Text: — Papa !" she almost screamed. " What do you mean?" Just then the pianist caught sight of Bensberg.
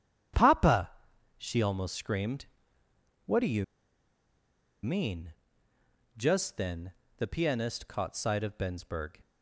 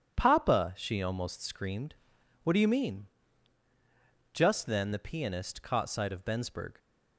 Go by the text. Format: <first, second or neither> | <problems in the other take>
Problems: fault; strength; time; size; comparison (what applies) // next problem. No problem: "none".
second | starts louder than the rest; strong; until 1.5 s; 9 dB; strong in the second // pauses between "you" and "mean"; at 3.6 s; 1.1 s long // pauses between "then" and "the"; slight; at 6.9 s; 0.26 s long